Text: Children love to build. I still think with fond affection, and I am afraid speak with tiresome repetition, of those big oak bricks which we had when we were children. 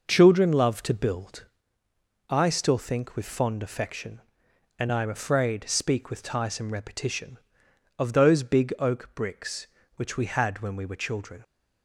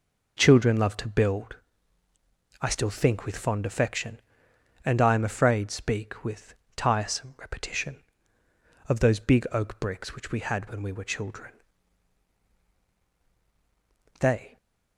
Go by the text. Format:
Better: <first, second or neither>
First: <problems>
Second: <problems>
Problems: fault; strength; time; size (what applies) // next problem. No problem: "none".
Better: first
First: none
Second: pauses between "with" and "tiresome"; slight; at 6.5 s; 0.24 s long // goes on to say "They"; slight; from 14.1 s on; 0.38 s long